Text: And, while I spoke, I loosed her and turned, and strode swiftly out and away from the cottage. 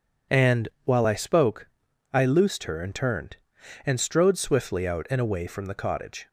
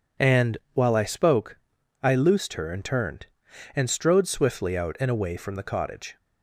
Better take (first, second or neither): neither